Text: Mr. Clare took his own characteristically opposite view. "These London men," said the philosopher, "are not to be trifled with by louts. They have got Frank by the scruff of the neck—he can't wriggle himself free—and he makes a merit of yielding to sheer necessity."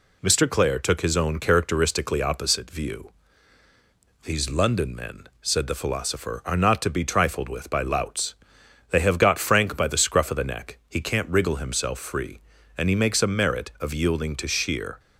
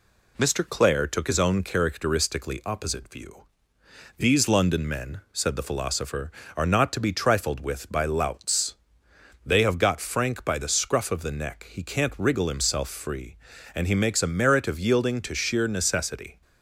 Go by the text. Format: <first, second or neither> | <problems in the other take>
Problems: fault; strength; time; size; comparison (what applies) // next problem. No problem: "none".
second | stops before "necessity"; at 14.9 s